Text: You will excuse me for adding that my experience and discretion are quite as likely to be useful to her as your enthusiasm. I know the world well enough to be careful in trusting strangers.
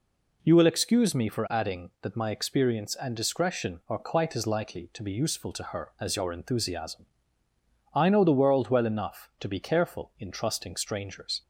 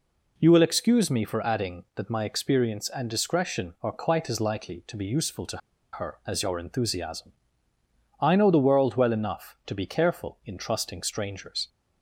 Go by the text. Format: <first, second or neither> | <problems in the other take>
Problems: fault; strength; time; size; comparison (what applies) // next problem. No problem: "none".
first | pauses between "to" and "her"; slight; at 5.5 s; 0.35 s long